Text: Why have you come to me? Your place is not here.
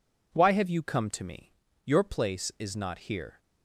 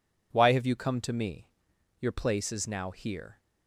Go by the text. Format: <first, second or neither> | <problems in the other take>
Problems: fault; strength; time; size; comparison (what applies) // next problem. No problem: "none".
first | says "now" for "not"; at 2.6 s